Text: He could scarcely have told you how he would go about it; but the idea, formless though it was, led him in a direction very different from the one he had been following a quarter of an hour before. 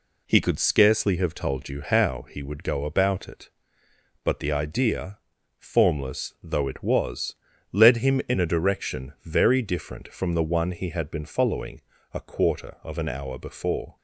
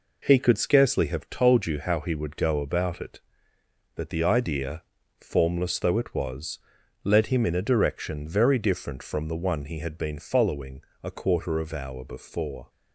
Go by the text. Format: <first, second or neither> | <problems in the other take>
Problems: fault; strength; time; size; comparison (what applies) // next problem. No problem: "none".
first | pauses between "following" and "a"; slight; at 10.8 s; 0.22 s long; slight in the first // skips "an"; at 11.7 s